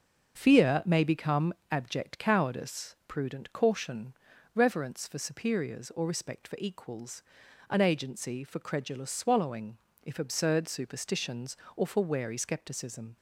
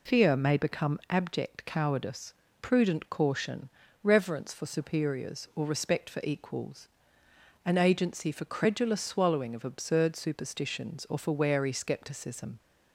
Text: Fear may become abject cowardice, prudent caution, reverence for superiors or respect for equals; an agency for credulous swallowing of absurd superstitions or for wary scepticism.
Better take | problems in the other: second | starts louder than the rest; until 1.3 s; 6.5 dB // pauses between "become" and "abject"; slight; at 1.5 s; 0.16 s long // says "if" for "of"; at 10.0 s

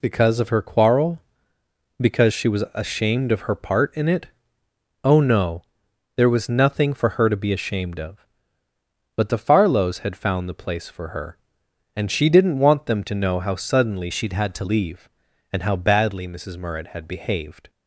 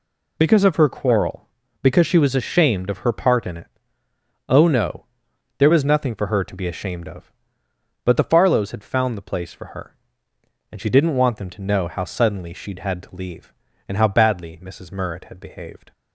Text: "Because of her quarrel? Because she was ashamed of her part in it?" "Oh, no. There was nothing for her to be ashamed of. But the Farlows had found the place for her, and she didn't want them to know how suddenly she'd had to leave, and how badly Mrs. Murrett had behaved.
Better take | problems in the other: second | changes voice from "she'd" to "to"; from 14.1 to 14.6 s; 0.5 s long

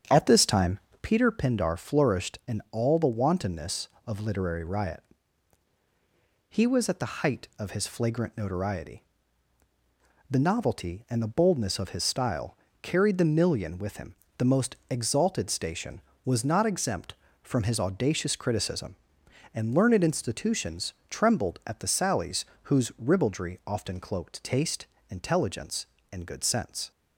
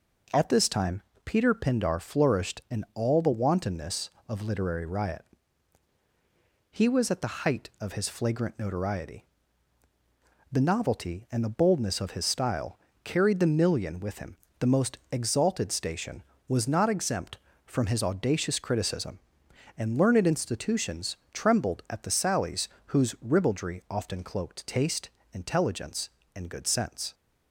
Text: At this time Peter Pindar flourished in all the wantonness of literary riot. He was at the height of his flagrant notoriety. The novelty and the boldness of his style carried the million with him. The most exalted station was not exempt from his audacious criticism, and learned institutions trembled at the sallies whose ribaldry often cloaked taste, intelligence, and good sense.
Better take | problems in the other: second | starts louder than the rest; strong; until 1.2 s; 8 dB // pauses between "time" and "Peter"; slight; at 0.7 s; 0.24 s long; slight in the second // pauses between "style" and "carried"; slight; at 12.5 s; 0.26 s long; slight in the second // pauses between "institutions" and "trembled"; slight; at 20.9 s; 0.16 s long; slight in the second // pauses between "sallies" and "whose"; slight; at 22.4 s; 0.20 s long; slight in the second

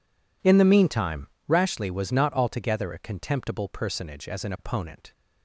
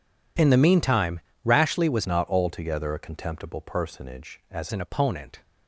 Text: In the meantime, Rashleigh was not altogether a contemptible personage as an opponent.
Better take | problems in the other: first | changes voice from "not" to "as"; from 2.0 to 4.6 s; 2.6 s long

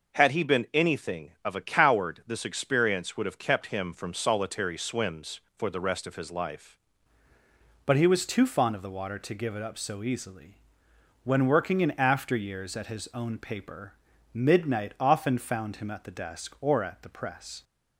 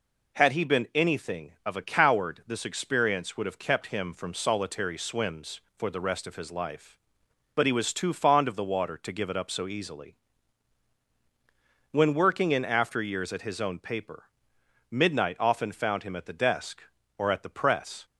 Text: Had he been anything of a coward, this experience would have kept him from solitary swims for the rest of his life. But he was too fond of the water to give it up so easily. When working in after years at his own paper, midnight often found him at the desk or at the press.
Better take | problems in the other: second | changes voice at "But"; from 7.8 s on; 9.8 s long

